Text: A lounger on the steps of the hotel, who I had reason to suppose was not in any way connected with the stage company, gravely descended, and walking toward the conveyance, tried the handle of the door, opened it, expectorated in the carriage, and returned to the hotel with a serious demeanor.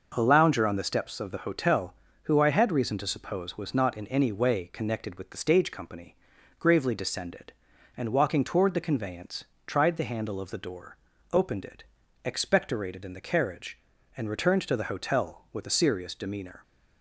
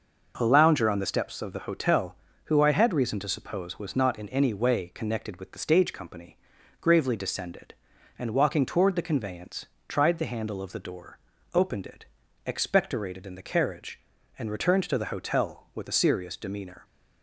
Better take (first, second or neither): neither